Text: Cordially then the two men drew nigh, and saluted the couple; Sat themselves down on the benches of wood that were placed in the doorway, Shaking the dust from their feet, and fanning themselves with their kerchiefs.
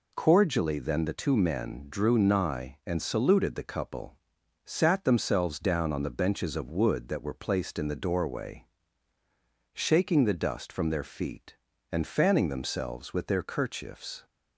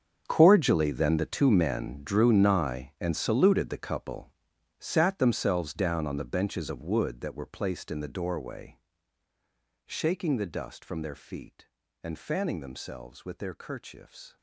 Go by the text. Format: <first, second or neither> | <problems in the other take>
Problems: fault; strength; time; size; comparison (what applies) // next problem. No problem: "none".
first | gets quieter; strong; throughout; 16 dB